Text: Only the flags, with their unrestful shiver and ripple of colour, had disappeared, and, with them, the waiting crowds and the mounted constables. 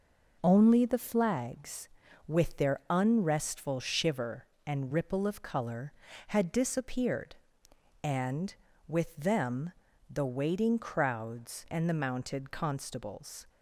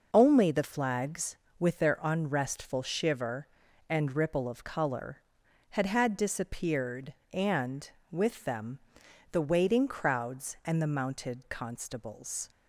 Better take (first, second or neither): first